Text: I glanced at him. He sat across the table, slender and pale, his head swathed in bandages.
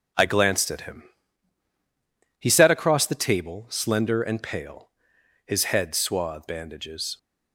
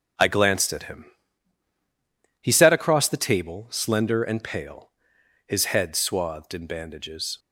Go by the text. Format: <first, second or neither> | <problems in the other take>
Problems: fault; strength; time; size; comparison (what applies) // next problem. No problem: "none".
second | skips "in"; at 6.4 s